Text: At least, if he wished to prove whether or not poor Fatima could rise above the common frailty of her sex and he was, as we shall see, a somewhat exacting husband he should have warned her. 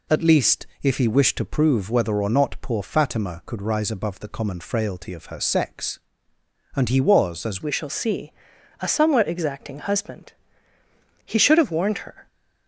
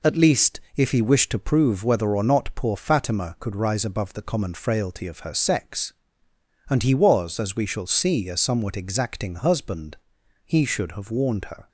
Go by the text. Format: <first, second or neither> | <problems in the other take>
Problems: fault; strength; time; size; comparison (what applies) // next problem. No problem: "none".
second | changes voice at "we"; from 7.6 s on; 4.6 s long // pauses between "husband" and "he"; noticeable; at 10.3 s; 0.92 s long; noticeable in the second